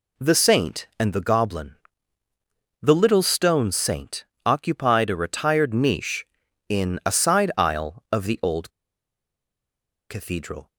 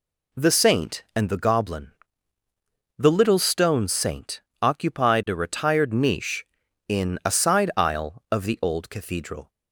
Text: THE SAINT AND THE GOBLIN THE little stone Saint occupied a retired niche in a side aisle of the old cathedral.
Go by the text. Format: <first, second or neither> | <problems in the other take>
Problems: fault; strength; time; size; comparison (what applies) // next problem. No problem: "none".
second | pauses between "GOBLIN" and "THE"; at 1.7 s; 1.0 s long; also in the second // pauses between "Saint" and "occupied"; slight; at 4.2 s; 0.22 s long; slight in the second // pauses between "old" and "cathedral"; strong; at 8.6 s; 1.3 s long